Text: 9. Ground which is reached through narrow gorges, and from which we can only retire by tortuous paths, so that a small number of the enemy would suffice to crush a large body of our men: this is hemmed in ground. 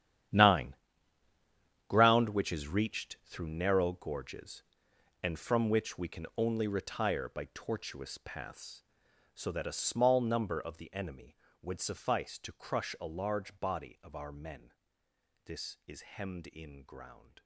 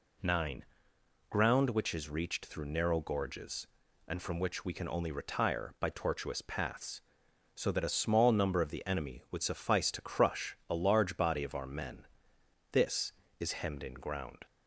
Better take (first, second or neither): second